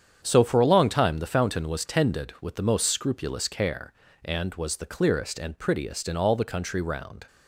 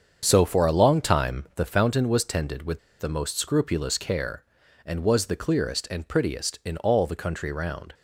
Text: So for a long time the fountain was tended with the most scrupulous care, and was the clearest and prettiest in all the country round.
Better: first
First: starts louder than the rest; strong; until 1.2 s; 8 dB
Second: starts louder than the rest; strong; until 1.2 s; 7 dB // pauses between "with" and "the"; slight; at 2.7 s; 0.20 s long

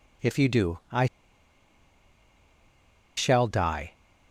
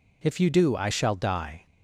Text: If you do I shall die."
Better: second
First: pauses between "I" and "shall"; strong; at 1.0 s; 2.1 s long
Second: none

